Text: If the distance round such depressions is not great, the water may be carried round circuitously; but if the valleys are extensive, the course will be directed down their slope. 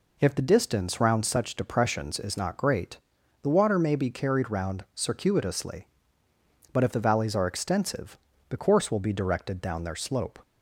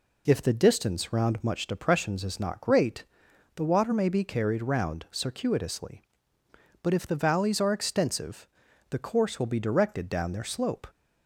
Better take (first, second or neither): first